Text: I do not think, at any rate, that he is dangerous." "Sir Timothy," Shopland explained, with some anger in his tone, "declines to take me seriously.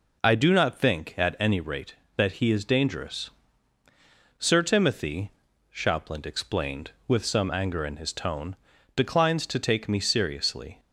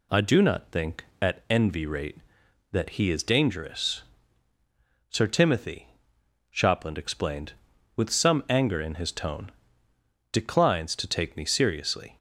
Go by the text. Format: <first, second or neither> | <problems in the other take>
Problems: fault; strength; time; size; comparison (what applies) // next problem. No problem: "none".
first | says "envy" for "any"; at 1.4 s